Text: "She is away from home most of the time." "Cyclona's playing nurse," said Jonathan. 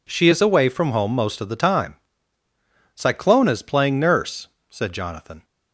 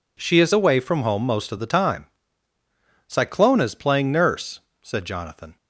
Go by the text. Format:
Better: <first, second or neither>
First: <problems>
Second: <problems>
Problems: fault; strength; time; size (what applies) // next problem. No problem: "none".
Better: neither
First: none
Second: none